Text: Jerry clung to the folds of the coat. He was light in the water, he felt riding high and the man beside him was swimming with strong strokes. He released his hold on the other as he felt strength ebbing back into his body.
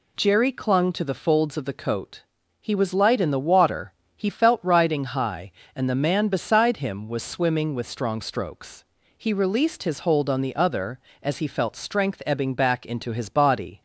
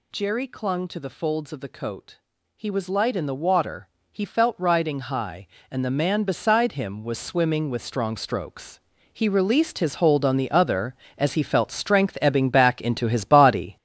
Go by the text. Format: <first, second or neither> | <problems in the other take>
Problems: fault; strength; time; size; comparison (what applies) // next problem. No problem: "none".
first | gets louder; strong; throughout; 7.5 dB